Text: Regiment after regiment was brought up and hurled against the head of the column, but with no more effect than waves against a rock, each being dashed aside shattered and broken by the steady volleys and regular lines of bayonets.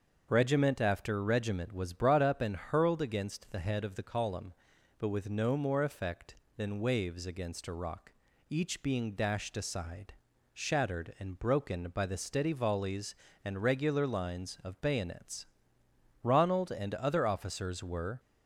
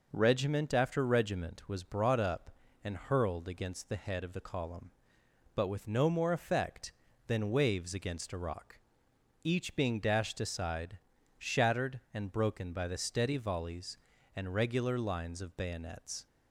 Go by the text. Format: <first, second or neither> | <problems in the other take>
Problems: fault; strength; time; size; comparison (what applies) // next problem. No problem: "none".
second | starts louder than the rest; until 1.3 s; 6.5 dB // pauses between "aside" and "shattered"; at 10.1 s; 0.38 s long; also in the second // goes on to say "Ronald and other officers were"; strong; from 16.2 s on; 1.9 s long